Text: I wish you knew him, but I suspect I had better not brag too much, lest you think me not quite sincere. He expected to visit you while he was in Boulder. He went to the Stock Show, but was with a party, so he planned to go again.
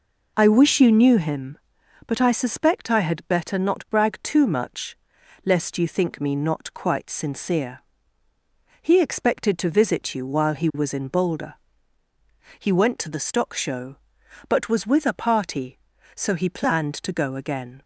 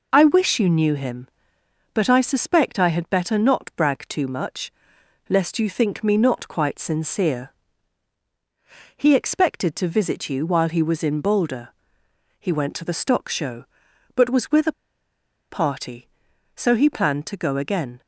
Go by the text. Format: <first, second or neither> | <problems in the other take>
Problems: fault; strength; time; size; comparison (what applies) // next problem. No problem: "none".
first | pauses between "a" and "party"; noticeable; at 14.7 s; 0.77 s long